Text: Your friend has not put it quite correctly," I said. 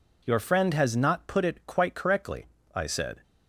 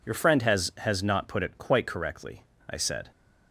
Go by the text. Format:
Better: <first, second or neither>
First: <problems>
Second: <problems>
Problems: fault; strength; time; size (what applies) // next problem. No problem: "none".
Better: first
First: none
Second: says "has" twice; at 0.7 s